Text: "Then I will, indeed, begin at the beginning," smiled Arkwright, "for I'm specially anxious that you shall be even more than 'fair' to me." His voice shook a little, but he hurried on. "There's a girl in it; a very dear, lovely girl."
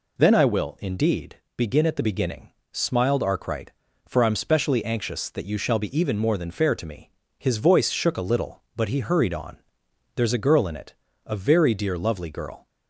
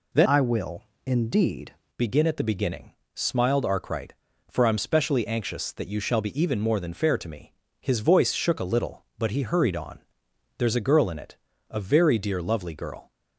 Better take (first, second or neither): first